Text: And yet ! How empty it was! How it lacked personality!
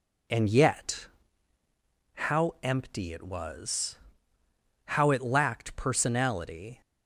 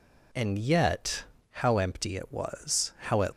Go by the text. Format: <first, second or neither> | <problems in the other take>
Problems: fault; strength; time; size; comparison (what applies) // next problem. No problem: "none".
first | stops before "lacked personality"; at 3.3 s